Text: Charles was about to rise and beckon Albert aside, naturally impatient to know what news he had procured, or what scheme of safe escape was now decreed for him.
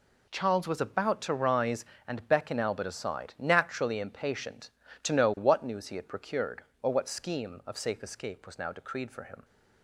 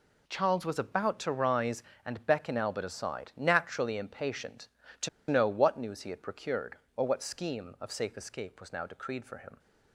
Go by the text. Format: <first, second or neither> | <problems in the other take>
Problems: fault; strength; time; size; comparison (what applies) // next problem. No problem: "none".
first | pauses between "to" and "know"; slight; at 5.0 s; 0.21 s long